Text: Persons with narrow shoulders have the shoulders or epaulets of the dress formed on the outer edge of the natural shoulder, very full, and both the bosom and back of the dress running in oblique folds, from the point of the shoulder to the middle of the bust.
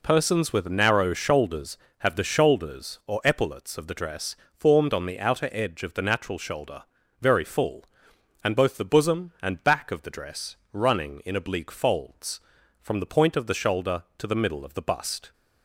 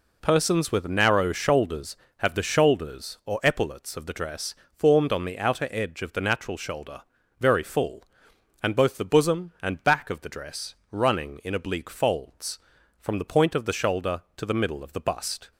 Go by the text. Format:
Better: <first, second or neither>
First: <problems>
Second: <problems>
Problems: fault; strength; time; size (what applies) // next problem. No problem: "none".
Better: neither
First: pauses between "dress" and "formed"; slight; at 4.3 s; 0.16 s long // pauses between "dress" and "running"; slight; at 10.5 s; 0.16 s long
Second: pauses between "dress" and "formed"; slight; at 4.5 s; 0.16 s long // pauses between "dress" and "running"; slight; at 10.7 s; 0.16 s long